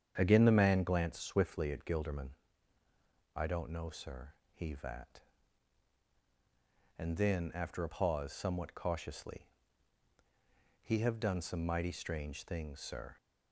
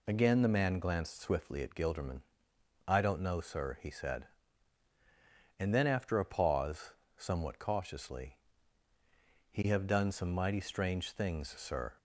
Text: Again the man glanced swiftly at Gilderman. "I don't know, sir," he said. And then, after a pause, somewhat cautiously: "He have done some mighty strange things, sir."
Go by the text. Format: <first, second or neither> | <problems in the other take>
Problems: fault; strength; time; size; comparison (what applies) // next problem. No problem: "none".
second | starts louder than the rest; strong; until 1.1 s; 8 dB // says "vat" for "said"; at 4.7 s